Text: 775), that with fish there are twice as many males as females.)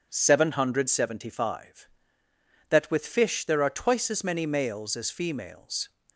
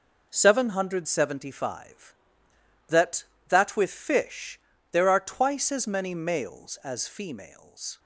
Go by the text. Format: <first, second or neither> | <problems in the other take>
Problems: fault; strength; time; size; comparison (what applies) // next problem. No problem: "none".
first | says "that" twice; at 3.4 s // pauses between "fish" and "there"; slight; at 4.5 s; 0.32 s long